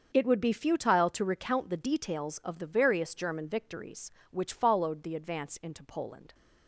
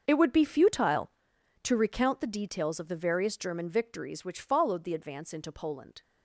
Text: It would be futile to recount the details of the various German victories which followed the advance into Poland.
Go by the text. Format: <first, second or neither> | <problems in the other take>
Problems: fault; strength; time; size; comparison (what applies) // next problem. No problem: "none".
first | gets quieter; strong; throughout; 15.5 dB // starts louder than the rest; until 1.0 s; 6.5 dB; also in the first